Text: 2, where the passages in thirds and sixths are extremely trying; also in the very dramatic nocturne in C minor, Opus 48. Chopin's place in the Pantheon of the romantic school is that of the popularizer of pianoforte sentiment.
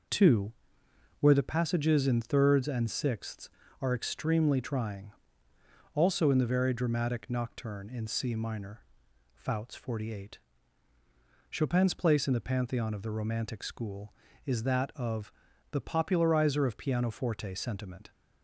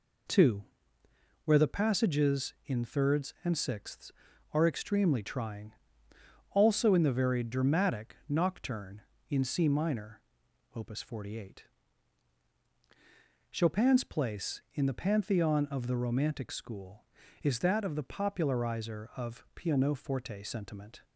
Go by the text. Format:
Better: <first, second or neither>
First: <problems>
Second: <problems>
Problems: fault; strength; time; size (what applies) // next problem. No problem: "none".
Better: second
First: says "Fouts" for "Opus"; at 9.3 s // pauses between "of" and "the"; at 15.3 s; 0.40 s long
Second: none